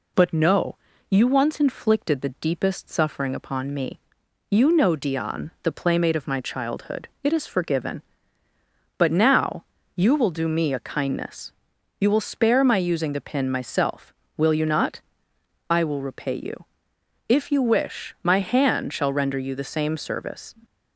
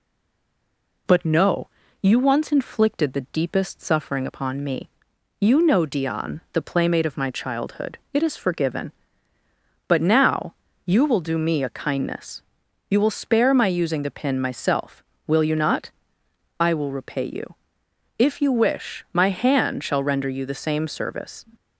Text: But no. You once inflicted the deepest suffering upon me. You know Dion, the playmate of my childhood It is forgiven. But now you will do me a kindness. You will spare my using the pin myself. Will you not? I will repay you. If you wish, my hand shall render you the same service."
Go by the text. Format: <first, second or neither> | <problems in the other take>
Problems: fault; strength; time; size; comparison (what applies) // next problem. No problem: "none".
first | stays silent before the first word; until 1.0 s; 1.0 s long // pauses between "now" and "you"; slight; at 10.5 s; 0.30 s long; slight in the first